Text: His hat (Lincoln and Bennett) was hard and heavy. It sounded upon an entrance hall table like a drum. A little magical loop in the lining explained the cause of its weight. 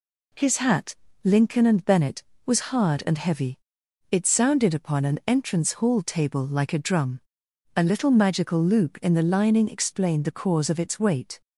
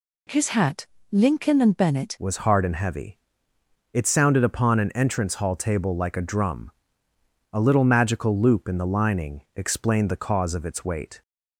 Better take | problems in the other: first | changes voice at "was"; from 2.1 s on; 9.1 s long

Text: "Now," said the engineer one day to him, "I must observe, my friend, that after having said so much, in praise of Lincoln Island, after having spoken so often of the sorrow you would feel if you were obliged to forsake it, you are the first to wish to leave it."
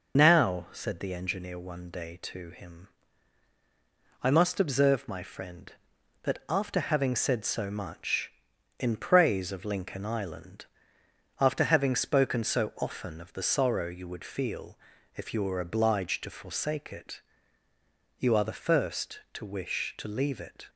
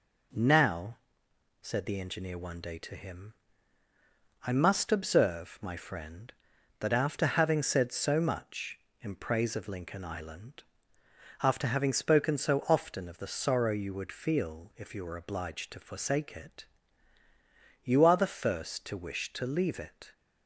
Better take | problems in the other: second | loses the start of "Now"; at 0.1 s; 65 ms // pauses between "feel" and "if"; at 14.7 s; 0.40 s long

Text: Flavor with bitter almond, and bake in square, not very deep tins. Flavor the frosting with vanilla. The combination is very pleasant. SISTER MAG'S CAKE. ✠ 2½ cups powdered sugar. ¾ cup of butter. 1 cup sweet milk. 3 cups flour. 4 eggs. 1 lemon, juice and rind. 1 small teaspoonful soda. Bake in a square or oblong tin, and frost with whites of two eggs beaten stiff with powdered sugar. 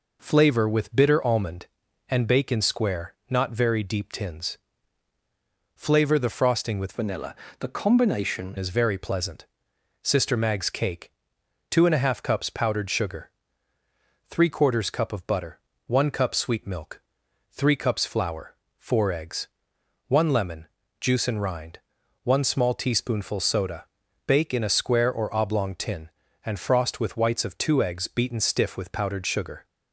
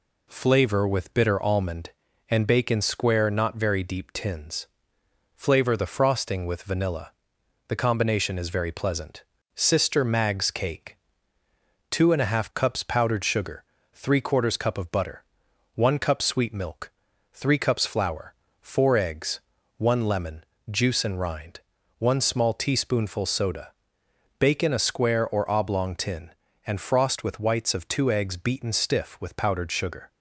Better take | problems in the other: second | changes voice from "vanilla" to "combination"; from 6.9 to 8.5 s; 1.6 s long

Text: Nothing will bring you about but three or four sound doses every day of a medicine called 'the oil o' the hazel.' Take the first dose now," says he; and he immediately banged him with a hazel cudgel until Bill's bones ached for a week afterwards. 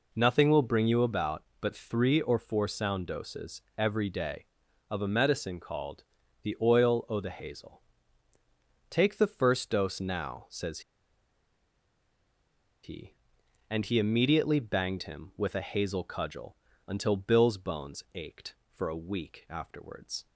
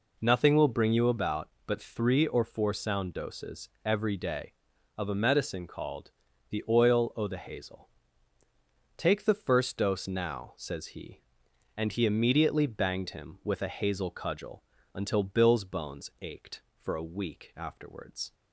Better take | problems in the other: second | pauses between "doses" and "every"; slight; at 3.6 s; 0.16 s long; slight in the second // pauses between "called" and "the"; at 6.0 s; 0.38 s long; also in the second // pauses between "says" and "he"; strong; at 10.7 s; 2.0 s long // pauses between "cudgel" and "until"; slight; at 16.5 s; 0.32 s long; slight in the second

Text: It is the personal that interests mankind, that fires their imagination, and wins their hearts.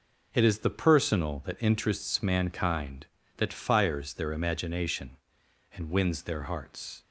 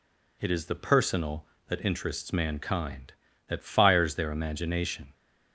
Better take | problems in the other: first | stops before "and wins their hearts"; at 5.1 s

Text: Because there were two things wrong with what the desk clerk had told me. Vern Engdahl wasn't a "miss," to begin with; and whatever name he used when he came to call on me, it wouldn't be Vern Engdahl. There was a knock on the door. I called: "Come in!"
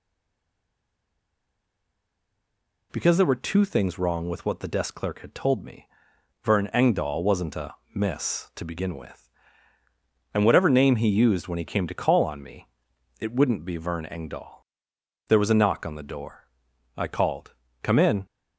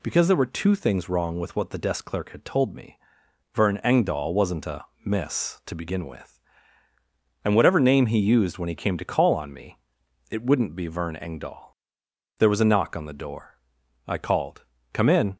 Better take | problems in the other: second | stays silent before the first word; strong; until 2.9 s; 2.9 s long // pauses between "a" and "miss"; slight; at 7.7 s; 0.20 s long; slight in the second

